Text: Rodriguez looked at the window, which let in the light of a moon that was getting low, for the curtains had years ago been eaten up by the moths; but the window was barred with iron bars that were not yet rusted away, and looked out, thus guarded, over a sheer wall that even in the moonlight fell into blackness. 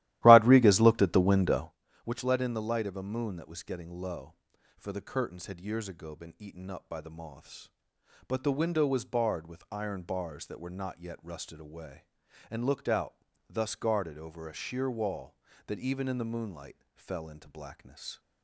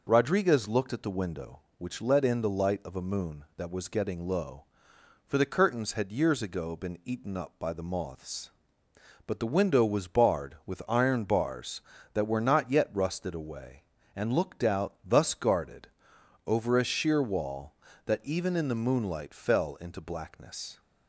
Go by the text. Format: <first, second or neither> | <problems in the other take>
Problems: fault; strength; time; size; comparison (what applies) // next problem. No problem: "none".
second | starts louder than the rest; strong; until 1.7 s; 15 dB // pauses between "moonlight" and "fell"; slight; at 16.7 s; 0.18 s long